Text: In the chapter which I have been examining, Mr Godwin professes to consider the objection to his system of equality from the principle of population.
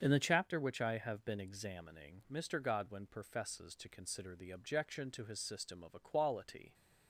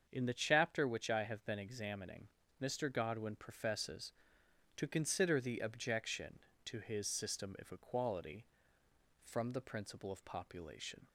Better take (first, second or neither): second